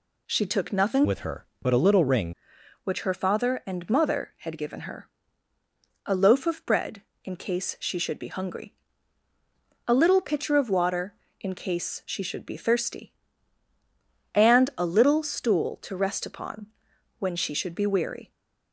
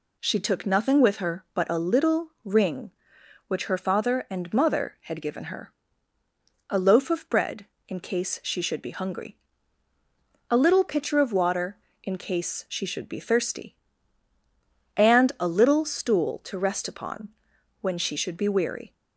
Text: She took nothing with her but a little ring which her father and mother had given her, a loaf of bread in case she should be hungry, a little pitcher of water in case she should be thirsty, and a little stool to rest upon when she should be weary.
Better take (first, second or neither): second